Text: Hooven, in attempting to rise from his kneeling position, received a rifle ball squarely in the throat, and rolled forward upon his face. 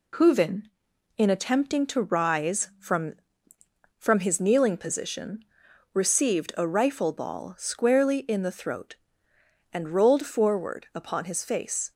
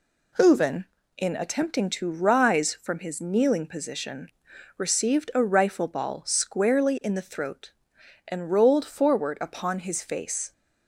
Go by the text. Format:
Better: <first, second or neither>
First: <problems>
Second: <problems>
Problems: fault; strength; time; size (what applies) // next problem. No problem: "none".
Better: second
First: says "from" twice; at 3.9 s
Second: none